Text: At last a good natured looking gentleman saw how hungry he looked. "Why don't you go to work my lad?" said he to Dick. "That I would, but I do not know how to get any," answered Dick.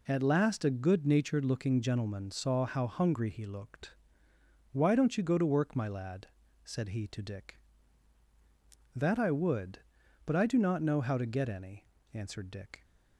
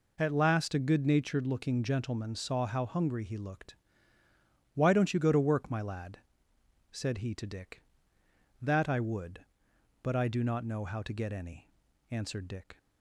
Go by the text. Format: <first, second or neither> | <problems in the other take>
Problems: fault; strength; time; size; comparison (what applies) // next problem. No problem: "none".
neither | none